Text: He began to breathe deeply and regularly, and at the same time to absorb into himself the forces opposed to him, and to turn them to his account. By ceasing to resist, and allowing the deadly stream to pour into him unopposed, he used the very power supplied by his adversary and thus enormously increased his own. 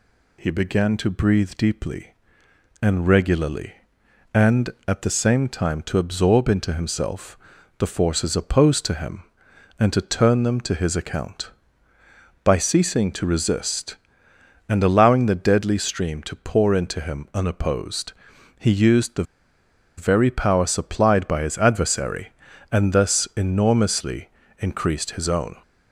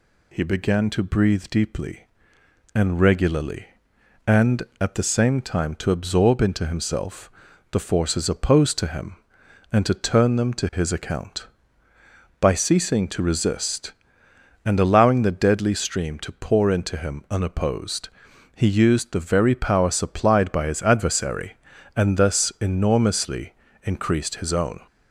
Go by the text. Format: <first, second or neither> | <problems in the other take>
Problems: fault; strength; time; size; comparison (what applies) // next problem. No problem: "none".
second | pauses between "himself" and "the"; at 7.3 s; 0.40 s long; also in the second // pauses between "the" and "very"; noticeable; at 19.2 s; 0.74 s long // pauses between "enormously" and "increased"; slight; at 24.2 s; 0.30 s long; slight in the second